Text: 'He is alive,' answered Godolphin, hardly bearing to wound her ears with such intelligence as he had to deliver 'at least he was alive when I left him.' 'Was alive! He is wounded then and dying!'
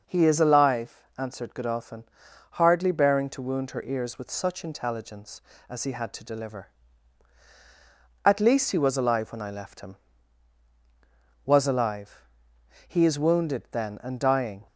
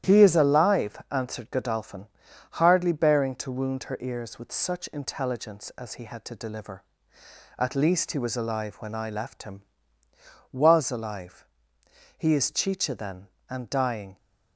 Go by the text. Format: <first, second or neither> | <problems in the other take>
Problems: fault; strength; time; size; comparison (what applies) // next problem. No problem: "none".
first | starts louder than the rest; strong; until 1.1 s; 11 dB // says "chicha" for "wounded"; at 12.5 s